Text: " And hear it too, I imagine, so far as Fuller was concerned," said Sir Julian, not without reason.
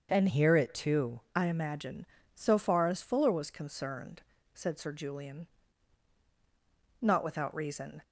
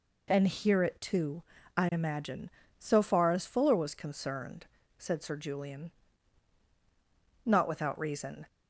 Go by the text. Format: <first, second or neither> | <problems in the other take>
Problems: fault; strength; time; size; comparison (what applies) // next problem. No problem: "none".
second | starts louder than the rest; until 1.1 s; 6.5 dB // changes voice from "hear" to "too"; from 0.2 to 1.2 s; 1.0 s long